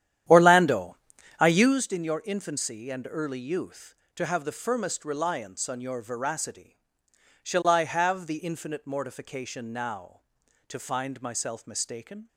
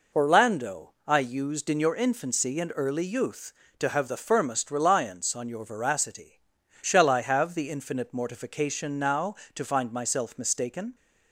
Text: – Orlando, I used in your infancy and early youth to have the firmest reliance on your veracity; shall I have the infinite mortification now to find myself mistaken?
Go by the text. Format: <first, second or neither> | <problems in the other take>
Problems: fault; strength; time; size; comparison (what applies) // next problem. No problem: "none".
second | starts louder than the rest; strong; until 1.9 s; 11 dB